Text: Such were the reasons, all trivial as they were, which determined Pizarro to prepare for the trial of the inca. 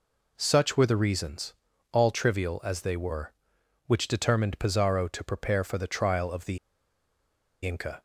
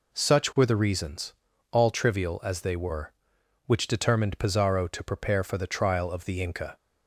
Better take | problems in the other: second | pauses between "the" and "inca"; at 6.5 s; 1.0 s long

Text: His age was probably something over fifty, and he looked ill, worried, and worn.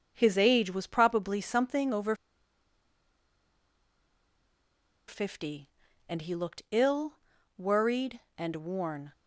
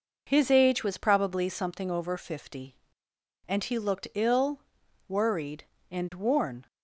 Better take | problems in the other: second | pauses between "over" and "fifty"; strong; at 2.1 s; 2.9 s long

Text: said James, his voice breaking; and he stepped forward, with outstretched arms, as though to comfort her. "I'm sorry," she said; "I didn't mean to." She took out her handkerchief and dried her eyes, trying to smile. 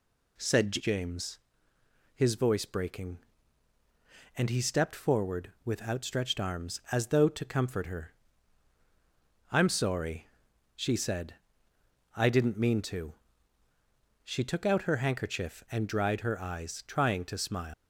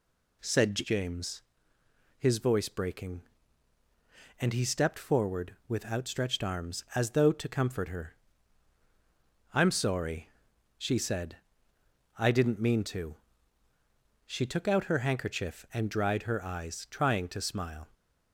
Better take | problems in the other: second | leaves "smile" unfinished; at 17.7 s; 165 ms

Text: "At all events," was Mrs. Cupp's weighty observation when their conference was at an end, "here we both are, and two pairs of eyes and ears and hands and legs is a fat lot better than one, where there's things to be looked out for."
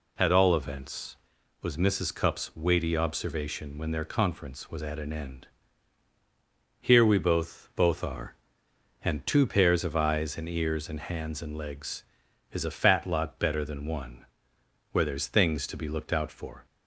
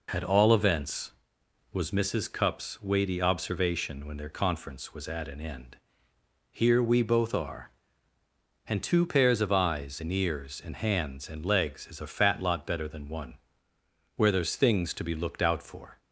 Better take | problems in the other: second | says "both" twice; at 7.7 s

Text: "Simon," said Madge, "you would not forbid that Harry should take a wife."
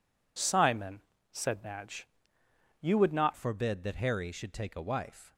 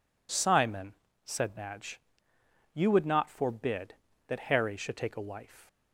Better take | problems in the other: second | changes voice at "forbid"; from 3.3 s on; 2.0 s long

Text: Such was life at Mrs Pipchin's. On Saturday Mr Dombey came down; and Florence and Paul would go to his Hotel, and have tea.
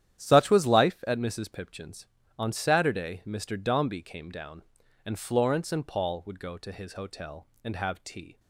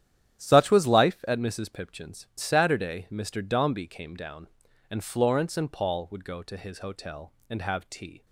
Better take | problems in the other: first | starts louder than the rest; strong; until 1.4 s; 11 dB; strong in the first // skips "On"; at 2.3 s

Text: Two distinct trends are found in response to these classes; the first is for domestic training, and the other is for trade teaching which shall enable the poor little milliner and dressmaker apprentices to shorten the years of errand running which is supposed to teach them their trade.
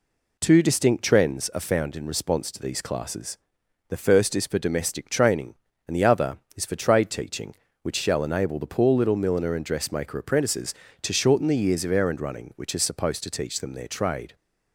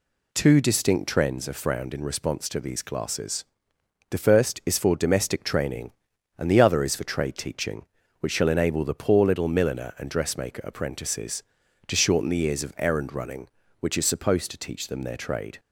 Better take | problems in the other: first | says "frowned" for "found"; at 1.6 s

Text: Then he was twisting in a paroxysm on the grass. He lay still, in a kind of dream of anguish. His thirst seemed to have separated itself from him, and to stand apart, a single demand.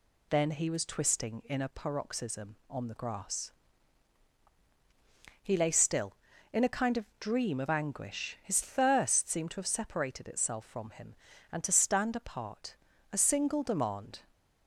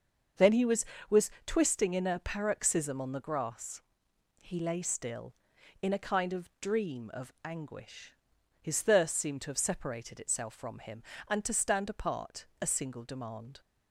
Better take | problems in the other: first | starts louder than the rest; until 1.7 s; 6.5 dB // says "was" twice; at 1.1 s

